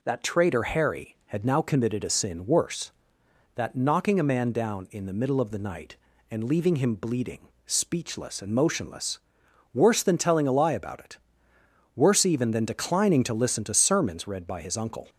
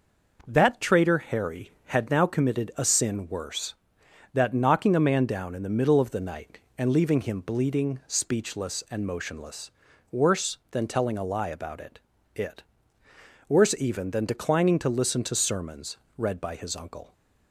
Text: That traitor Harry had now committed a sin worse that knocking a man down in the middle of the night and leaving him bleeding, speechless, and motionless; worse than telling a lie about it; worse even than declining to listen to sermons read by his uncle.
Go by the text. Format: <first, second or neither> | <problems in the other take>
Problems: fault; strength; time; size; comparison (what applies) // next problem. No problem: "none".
first | says "it" twice; at 12.3 s // pauses between "sermons" and "read"; slight; at 15.9 s; 0.18 s long